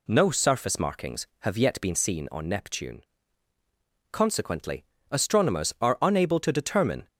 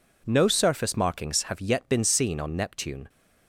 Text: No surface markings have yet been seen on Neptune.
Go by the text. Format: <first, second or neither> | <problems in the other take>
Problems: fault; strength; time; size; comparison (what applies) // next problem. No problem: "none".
second | goes on to say "Consequently astronomers are unable to determine"; strong; from 4.1 s on; 2.9 s long